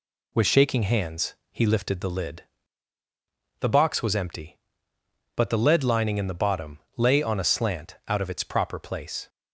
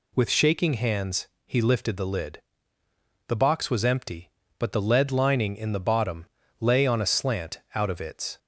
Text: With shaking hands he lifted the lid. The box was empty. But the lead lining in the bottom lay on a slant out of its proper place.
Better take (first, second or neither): first